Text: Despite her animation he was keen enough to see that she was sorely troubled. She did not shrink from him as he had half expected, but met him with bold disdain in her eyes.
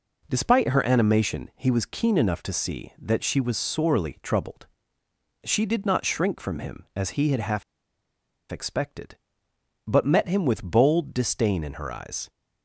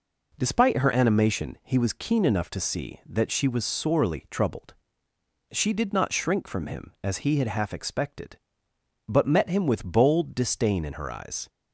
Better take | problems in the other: second | pauses between "half" and "expected"; noticeable; at 7.6 s; 0.89 s long

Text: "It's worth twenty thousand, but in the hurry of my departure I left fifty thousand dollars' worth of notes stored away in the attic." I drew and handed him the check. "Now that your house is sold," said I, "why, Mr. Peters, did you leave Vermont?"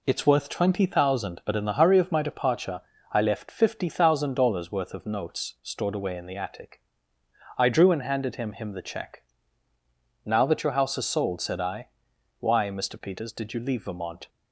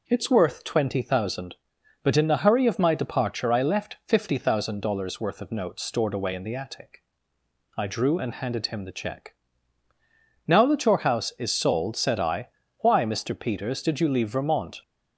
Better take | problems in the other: second | pauses between "departure" and "I"; slight; at 2.8 s; 0.32 s long // says "him" twice; at 8.5 s

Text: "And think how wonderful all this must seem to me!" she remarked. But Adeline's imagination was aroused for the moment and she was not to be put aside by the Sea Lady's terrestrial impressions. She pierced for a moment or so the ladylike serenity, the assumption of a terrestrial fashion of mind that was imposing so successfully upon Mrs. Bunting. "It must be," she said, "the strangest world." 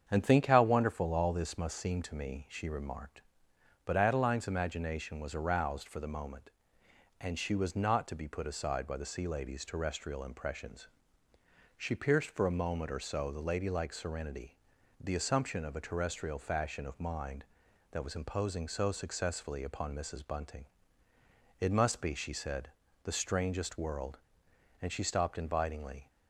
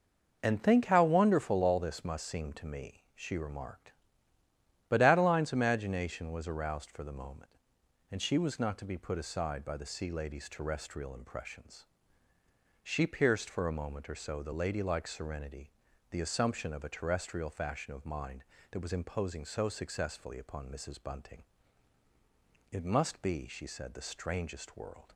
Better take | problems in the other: second | starts louder than the rest; strong; until 1.0 s; 7.5 dB // goes on to say "And she stopped invitingly"; noticeable; from 24.8 s on; 1.2 s long

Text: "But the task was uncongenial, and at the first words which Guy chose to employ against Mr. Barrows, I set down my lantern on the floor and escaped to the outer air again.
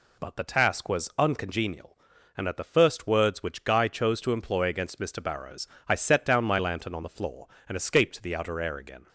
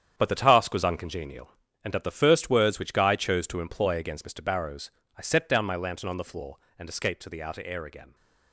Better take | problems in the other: first | gets quieter; strong; throughout; 9 dB

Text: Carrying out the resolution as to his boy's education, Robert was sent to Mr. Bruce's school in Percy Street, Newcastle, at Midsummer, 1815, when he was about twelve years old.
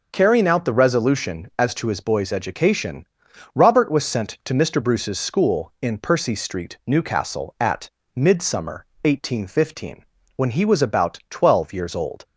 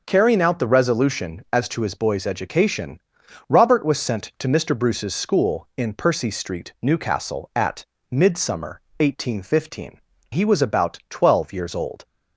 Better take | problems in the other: first | pauses between "at" and "Midsummer"; slight; at 7.8 s; 0.24 s long; slight in the first // skips "when"; at 10.1 s

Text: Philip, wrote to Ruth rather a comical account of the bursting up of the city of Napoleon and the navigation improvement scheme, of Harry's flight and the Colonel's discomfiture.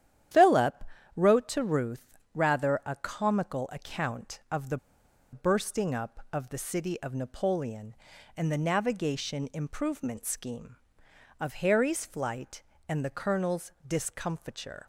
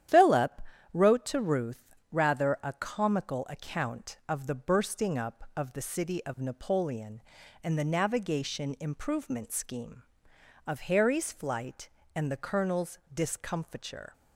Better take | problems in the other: second | starts louder than the rest; strong; until 1.6 s; 10.5 dB; strong in the second // pauses between "Ruth" and "rather"; slight; at 2.1 s; 0.18 s long; slight in the second // pauses between "the" and "bursting"; noticeable; at 4.7 s; 0.54 s long // pauses between "Colonel's" and "discomfiture"; slight; at 13.7 s; 0.16 s long; slight in the second

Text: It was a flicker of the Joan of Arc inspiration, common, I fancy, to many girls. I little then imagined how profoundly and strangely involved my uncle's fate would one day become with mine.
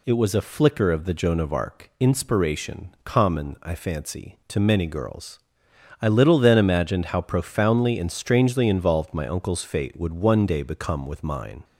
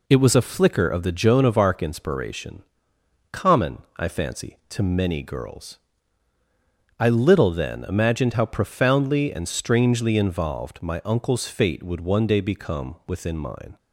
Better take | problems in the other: first | says "within" for "with"; at 13.0 s

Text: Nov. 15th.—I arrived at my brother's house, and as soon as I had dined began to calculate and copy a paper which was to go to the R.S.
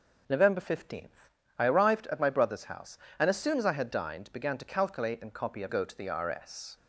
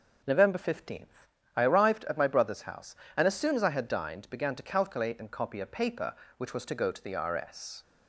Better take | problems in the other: second | skips "paper which was to"; at 5.6 s

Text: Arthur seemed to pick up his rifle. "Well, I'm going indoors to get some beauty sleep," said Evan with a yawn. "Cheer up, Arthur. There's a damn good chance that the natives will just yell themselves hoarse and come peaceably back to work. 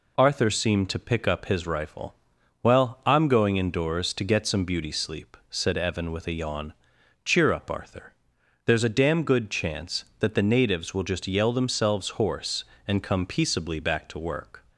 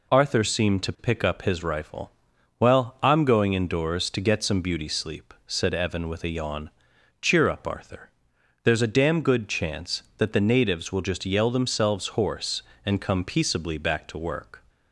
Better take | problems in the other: neither | none

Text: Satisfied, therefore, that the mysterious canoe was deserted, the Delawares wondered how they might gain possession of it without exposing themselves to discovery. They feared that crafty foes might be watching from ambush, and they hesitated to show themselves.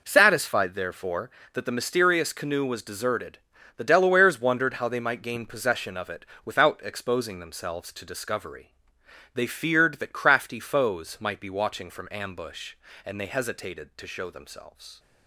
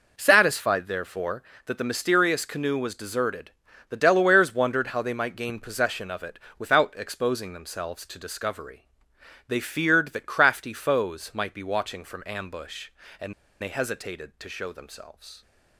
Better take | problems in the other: first | pauses between "it" and "without"; slight; at 6.3 s; 0.20 s long; slight in the first // pauses between "and" and "they"; slight; at 13.3 s; 0.29 s long

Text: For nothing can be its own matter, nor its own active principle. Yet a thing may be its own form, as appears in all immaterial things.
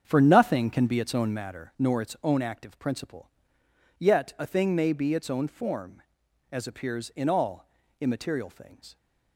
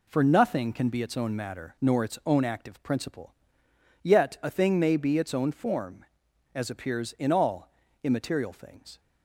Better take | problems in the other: second | starts louder than the rest; strong; until 1.5 s; 7.5 dB // pauses between "all" and "immaterial"; slight; at 7.6 s; 0.34 s long; slight in the second

